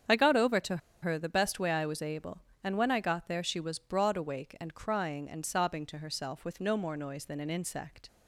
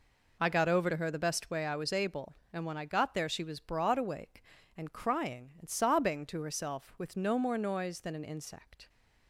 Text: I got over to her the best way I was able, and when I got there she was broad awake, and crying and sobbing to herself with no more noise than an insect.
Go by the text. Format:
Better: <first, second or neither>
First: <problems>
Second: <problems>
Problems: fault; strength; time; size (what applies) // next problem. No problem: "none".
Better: second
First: starts louder than the rest; strong; until 1.3 s; 8 dB // pauses between "to" and "her"; slight; at 0.7 s; 0.24 s long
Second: none